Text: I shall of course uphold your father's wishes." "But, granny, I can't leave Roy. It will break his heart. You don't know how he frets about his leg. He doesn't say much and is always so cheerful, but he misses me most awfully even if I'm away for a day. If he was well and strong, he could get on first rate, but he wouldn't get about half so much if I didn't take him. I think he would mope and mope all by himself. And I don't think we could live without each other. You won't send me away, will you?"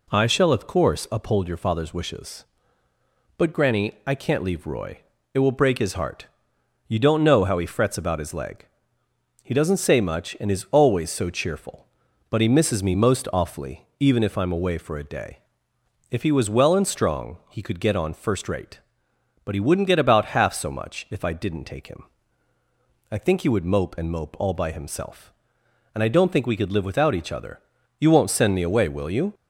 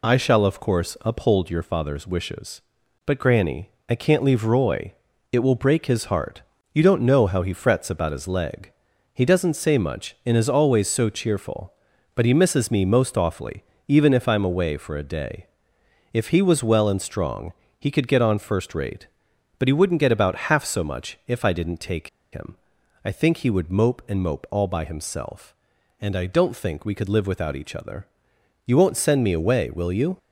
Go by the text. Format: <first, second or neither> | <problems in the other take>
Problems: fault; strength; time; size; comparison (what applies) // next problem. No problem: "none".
first | pauses between "awfully" and "even"; slight; at 13.6 s; 0.26 s long // pauses between "take" and "him"; slight; at 22.0 s; 0.23 s long